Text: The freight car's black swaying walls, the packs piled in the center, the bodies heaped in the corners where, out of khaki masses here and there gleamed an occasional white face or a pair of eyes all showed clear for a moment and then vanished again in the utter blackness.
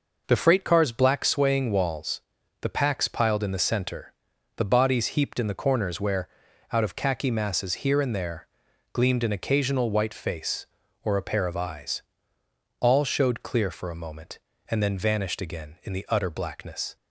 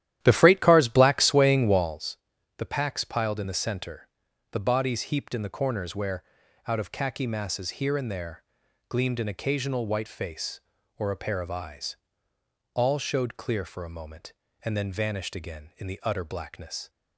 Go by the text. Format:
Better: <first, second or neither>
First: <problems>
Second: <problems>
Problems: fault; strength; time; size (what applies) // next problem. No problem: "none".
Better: first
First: pauses between "there" and "gleamed"; noticeable; at 8.4 s; 0.46 s long // pauses between "eyes" and "all"; noticeable; at 12.0 s; 0.78 s long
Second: starts louder than the rest; strong; until 2.0 s; 12 dB // pauses between "there" and "gleamed"; noticeable; at 8.4 s; 0.46 s long // pauses between "eyes" and "all"; noticeable; at 11.9 s; 0.78 s long